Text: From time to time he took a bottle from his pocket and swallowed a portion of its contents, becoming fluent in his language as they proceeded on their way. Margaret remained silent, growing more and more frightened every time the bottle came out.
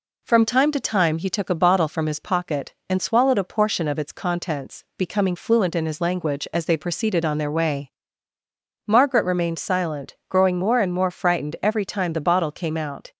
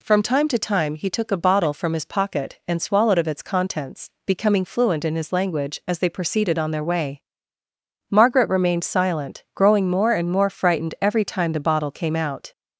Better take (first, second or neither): first